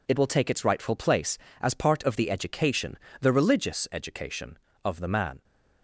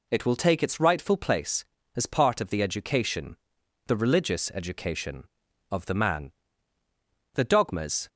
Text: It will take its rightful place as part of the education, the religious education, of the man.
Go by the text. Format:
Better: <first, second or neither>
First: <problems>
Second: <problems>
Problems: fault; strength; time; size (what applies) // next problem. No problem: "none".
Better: first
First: none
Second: goes on to say "The dogmas"; noticeable; from 7.3 s on; 0.74 s long